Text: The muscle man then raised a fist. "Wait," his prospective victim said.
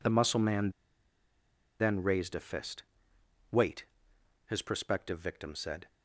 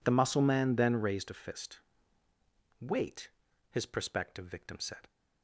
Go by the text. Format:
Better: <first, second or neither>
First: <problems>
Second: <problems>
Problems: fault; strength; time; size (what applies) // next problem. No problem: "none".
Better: second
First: pauses between "man" and "then"; at 0.6 s; 1.0 s long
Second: none